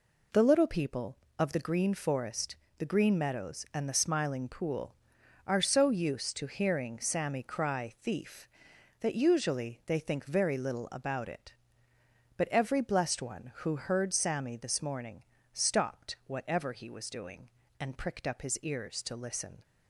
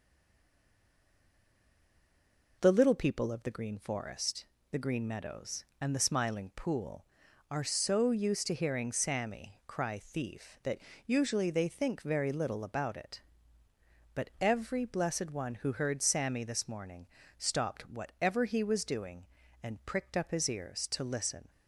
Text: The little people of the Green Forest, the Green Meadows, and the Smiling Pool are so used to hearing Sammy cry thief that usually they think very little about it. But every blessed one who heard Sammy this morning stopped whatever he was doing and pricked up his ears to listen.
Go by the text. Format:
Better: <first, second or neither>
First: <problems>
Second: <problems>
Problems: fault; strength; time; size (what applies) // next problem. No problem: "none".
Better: first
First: pauses between "morning" and "stopped"; slight; at 15.2 s; 0.30 s long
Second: stays silent before the first word; strong; until 2.5 s; 2.5 s long // pauses between "that" and "usually"; slight; at 10.7 s; 0.26 s long // pauses between "morning" and "stopped"; slight; at 17.0 s; 0.32 s long